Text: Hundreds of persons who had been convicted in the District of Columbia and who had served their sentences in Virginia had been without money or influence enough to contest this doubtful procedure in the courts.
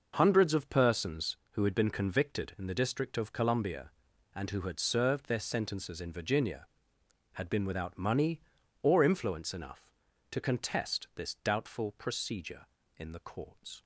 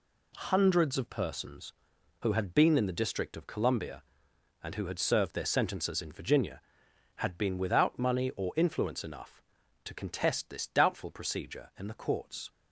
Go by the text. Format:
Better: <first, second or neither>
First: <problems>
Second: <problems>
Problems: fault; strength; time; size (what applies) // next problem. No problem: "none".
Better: first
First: none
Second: skips "convicted"; at 2.7 s